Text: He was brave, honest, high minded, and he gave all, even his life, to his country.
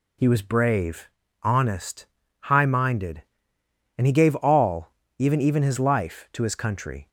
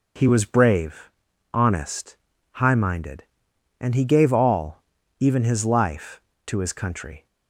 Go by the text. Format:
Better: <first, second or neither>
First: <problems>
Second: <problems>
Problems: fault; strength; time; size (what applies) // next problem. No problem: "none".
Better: second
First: says "even" twice; at 5.4 s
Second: none